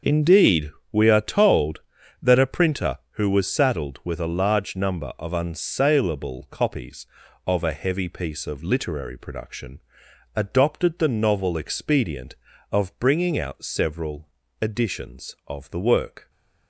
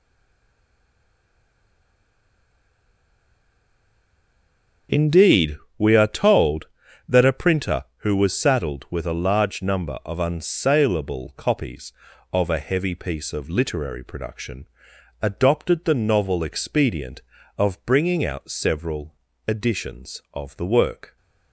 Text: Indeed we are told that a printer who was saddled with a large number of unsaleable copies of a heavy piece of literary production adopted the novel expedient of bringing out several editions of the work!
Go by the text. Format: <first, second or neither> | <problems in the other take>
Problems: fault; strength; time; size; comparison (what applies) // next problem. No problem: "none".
first | stays silent before the first word; strong; until 4.8 s; 4.8 s long // starts louder than the rest; until 6.1 s; 6.5 dB; also in the first // pauses between "Indeed" and "we"; slight; at 5.5 s; 0.22 s long; slight in the first // pauses between "production" and "adopted"; noticeable; at 14.6 s; 0.56 s long; noticeable in the first // pauses between "several" and "editions"; slight; at 19.1 s; 0.32 s long; slight in the first